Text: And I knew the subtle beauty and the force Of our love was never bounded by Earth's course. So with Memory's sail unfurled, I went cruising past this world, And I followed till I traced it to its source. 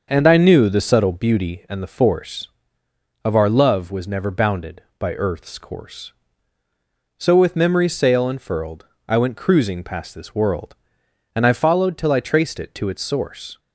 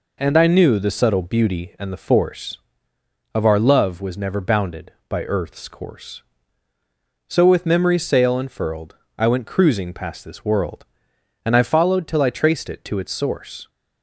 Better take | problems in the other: second | starts louder than the rest; until 1.1 s; 6.5 dB

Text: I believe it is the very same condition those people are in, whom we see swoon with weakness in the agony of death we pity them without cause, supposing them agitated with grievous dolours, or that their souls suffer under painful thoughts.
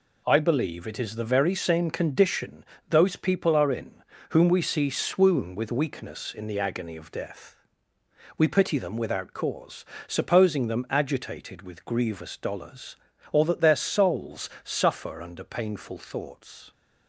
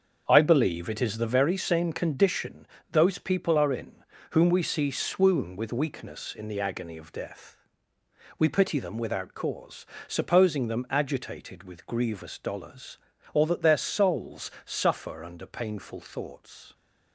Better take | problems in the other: first | starts louder than the rest; until 1.4 s; 7 dB // pauses between "condition" and "those"; slight; at 2.6 s; 0.24 s long; slight in the first // pauses between "death" and "we"; noticeable; at 7.5 s; 0.78 s long; noticeable in the first

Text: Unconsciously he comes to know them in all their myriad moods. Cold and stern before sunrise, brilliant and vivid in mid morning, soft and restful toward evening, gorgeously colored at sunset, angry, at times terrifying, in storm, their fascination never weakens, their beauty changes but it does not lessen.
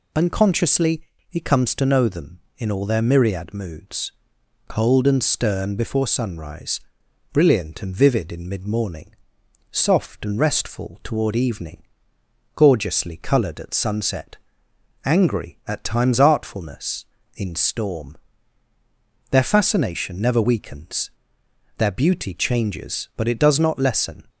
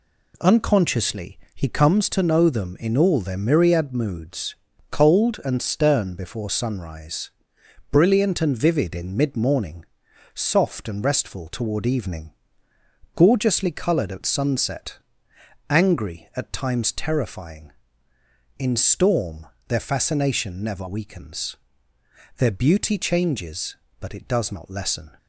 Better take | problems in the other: second | pauses between "Unconsciously" and "he"; slight; at 1.0 s; 0.26 s long; slight in the second // says "artfulness" for "terrifying"; at 16.2 s

